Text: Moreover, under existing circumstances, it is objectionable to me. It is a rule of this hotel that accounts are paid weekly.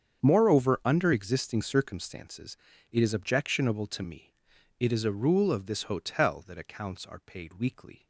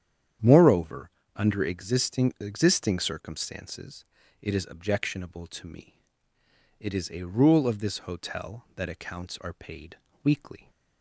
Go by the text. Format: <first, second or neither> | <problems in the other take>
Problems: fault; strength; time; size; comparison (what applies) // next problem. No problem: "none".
first | starts louder than the rest; strong; until 1.6 s; 9 dB; strong in the first // says "existing" twice; at 2.3 s // pauses between "paid" and "weekly"; slight; at 9.9 s; 0.26 s long